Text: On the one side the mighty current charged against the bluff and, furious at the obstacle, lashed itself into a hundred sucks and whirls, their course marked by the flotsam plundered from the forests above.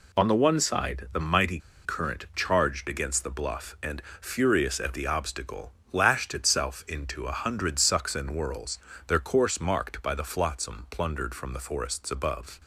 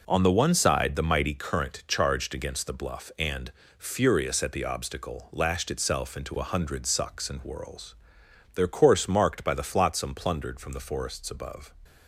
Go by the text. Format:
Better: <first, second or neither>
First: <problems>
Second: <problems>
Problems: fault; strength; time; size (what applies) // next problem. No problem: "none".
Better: second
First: pauses between "mighty" and "current"; slight; at 1.5 s; 0.27 s long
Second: none